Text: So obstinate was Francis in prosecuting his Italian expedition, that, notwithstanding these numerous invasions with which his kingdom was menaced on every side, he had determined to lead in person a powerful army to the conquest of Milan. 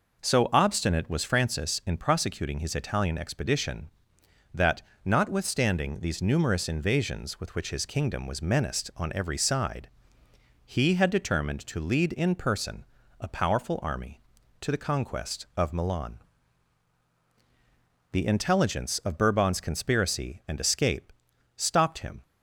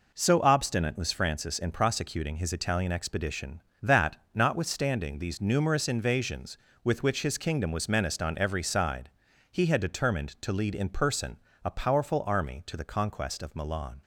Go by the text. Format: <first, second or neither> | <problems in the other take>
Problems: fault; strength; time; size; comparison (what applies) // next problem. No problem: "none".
second | pauses between "person" and "a"; slight; at 12.8 s; 0.36 s long; slight in the second // goes on to say "The intelligence of Bourbon's conspiracy and escape stopped him"; strong; from 18.1 s on; 4.1 s long